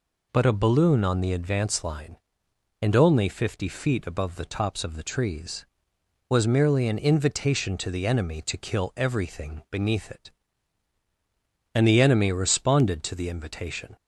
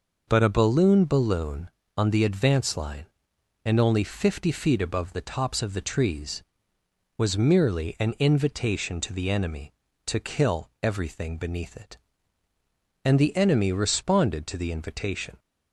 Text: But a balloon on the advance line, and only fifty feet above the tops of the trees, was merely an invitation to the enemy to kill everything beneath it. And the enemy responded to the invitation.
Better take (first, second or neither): first